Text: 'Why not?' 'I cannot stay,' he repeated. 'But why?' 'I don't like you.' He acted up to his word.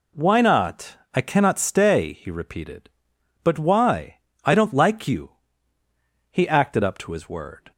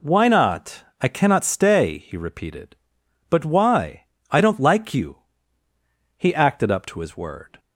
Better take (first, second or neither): neither